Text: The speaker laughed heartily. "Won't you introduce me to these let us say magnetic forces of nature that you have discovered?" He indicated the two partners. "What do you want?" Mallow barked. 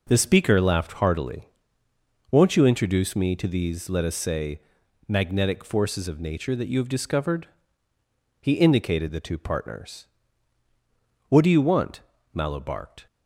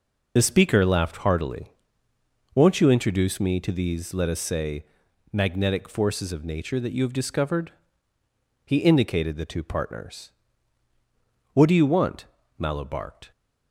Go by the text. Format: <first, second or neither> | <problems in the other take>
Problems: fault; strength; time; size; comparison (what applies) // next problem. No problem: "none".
first | loses the start of "The"; at 0.3 s; 45 ms // pauses between "say" and "magnetic"; at 4.8 s; 0.44 s long; also in the first